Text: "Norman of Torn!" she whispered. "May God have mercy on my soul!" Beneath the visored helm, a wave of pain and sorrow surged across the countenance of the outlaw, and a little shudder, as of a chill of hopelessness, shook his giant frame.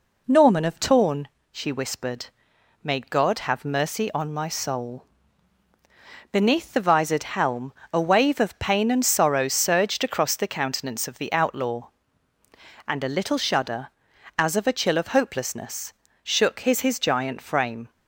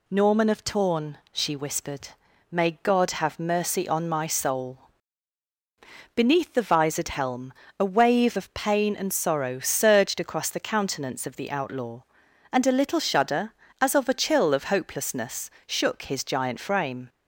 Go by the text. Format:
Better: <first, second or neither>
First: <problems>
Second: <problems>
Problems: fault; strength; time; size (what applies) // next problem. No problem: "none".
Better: second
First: says "his" twice; at 16.7 s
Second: none